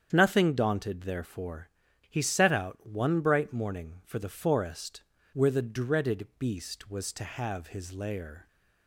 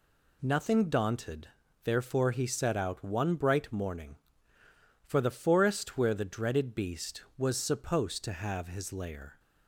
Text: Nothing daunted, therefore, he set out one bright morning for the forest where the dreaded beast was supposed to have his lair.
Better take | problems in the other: second | starts louder than the rest; strong; until 1.1 s; 8 dB // pauses between "forest" and "where"; slight; at 5.0 s; 0.30 s long // skips "supposed"; at 7.1 s

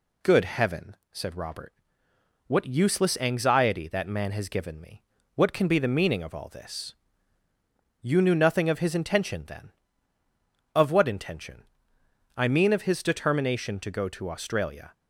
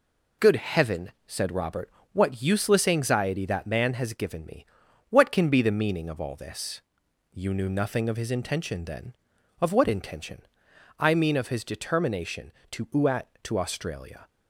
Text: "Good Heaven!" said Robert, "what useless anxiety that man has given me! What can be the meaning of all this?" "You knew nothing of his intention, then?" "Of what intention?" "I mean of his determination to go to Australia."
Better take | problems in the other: first | says "uat" for "go"; at 12.8 s

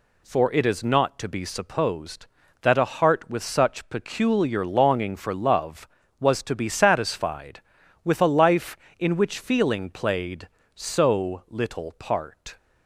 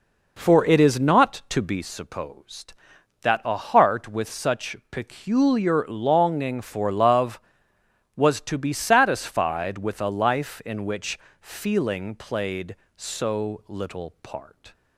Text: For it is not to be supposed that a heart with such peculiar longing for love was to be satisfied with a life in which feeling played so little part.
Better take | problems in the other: first | starts louder than the rest; noticeable; until 1.8 s; 4.5 dB // pauses between "such" and "peculiar"; slight; at 4.7 s; 0.16 s long // pauses between "which" and "feeling"; slight; at 11.1 s; 0.24 s long

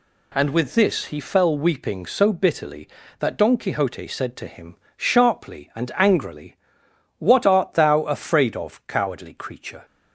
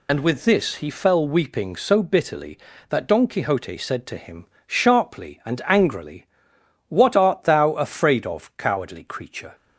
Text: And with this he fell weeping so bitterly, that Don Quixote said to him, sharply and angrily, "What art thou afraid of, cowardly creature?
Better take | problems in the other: first | loses the start of "And"; at 0.0 s; 75 ms

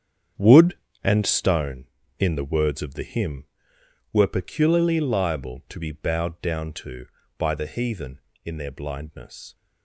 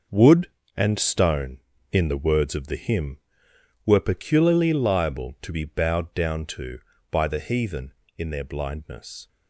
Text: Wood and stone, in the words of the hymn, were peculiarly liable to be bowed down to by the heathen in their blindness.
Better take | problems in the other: second | starts louder than the rest; strong; until 1.5 s; 8 dB

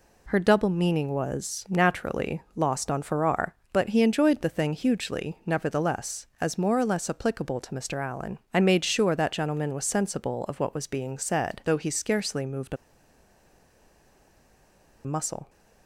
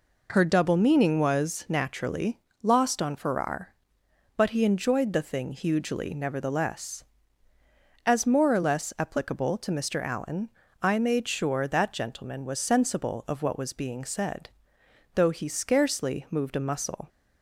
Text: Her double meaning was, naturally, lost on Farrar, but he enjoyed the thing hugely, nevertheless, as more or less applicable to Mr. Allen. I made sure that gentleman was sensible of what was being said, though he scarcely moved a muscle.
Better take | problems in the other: second | pauses between "a" and "muscle"; strong; at 12.7 s; 2.2 s long

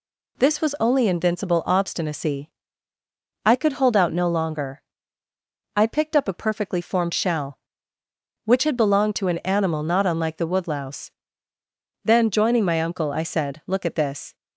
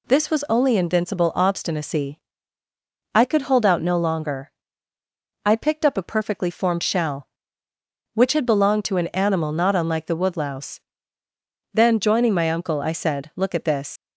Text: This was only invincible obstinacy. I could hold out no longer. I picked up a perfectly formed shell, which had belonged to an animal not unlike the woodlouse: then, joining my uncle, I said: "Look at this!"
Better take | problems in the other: first | leaves "this" unfinished; at 13.9 s; 85 ms

